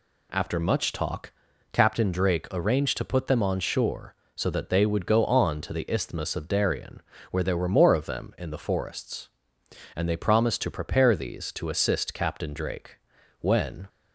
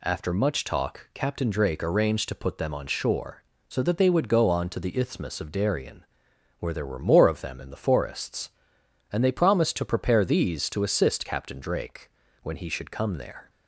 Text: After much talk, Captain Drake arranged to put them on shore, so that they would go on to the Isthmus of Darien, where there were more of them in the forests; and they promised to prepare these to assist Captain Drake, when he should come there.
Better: second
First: stops before "he should come there"; at 13.8 s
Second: none

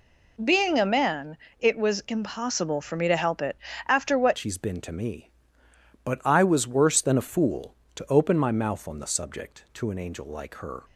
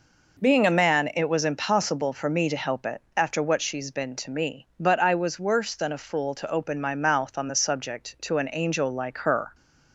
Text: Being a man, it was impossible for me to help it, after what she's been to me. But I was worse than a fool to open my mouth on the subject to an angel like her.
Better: second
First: changes voice at "she's"; from 4.3 s on; 6.5 s long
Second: none

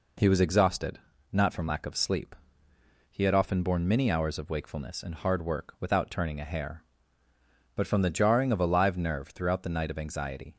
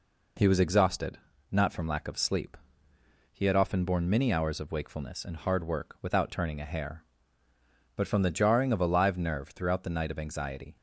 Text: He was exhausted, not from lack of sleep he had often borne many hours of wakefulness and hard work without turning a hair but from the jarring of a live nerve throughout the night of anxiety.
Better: neither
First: pauses between "sleep" and "he"; noticeable; at 2.3 s; 0.78 s long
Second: pauses between "sleep" and "he"; noticeable; at 2.5 s; 0.78 s long

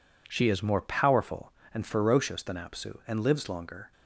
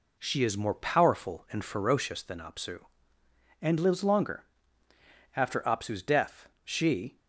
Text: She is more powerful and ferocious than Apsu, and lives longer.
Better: first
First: none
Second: goes on to say "After Apsu's death she"; strong; from 5.3 s on; 1.8 s long

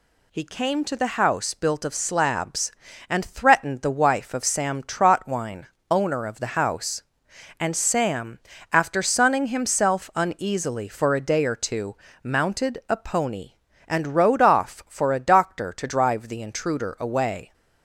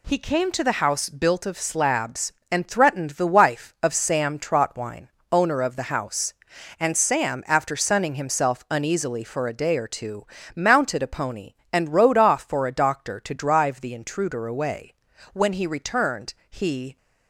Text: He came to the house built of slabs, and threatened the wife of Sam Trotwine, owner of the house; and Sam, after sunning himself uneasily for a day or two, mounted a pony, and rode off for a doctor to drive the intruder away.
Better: first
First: none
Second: goes on to say "When he returned he"; from 15.3 s on; 1.6 s long

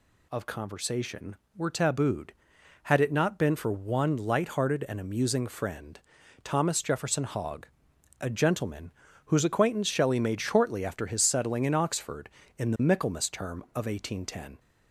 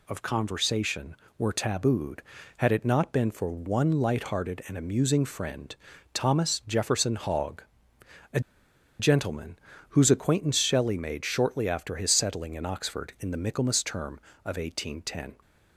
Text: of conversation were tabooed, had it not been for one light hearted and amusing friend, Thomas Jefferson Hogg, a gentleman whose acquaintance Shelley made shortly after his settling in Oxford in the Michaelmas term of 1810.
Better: first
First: pauses between "gentleman" and "whose"; slight; at 8.9 s; 0.34 s long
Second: pauses between "a" and "gentleman"; noticeable; at 8.3 s; 0.60 s long // pauses between "gentleman" and "whose"; slight; at 9.5 s; 0.32 s long

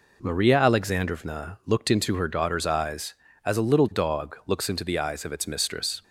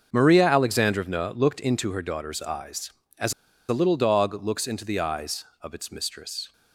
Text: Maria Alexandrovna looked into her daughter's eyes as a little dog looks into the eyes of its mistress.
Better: first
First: none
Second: starts louder than the rest; until 1.1 s; 6 dB // pauses between "as" and "a"; at 3.3 s; 0.36 s long

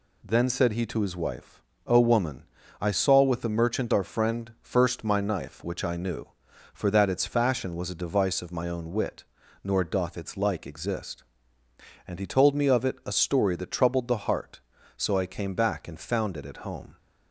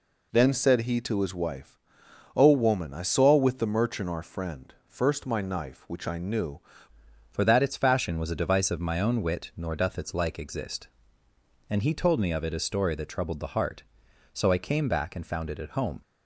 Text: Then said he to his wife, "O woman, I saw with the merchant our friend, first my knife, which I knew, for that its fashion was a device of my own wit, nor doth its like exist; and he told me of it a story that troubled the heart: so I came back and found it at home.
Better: first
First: none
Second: changes voice at "for"; from 7.3 s on; 8.7 s long

